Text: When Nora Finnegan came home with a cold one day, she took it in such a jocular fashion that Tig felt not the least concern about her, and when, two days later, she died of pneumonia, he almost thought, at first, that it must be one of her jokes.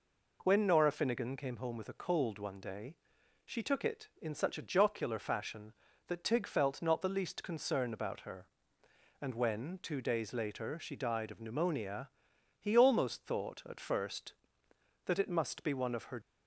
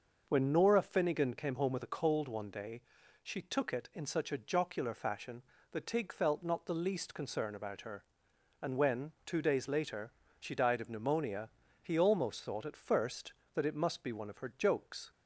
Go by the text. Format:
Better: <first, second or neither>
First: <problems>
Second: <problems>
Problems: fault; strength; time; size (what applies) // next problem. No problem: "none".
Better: second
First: stops before "jokes"; at 16.2 s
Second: none